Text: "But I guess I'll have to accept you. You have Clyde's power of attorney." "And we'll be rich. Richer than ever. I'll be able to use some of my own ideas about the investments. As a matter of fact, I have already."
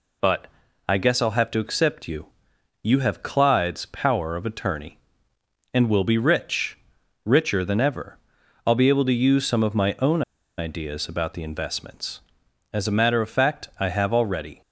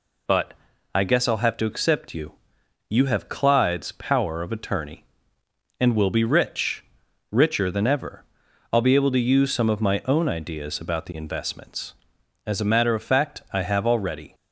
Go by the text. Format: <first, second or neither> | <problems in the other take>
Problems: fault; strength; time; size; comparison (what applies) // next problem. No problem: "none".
second | pauses between "But" and "I"; at 0.4 s; 0.38 s long; also in the second // pauses between "own" and "ideas"; at 10.2 s; 0.37 s long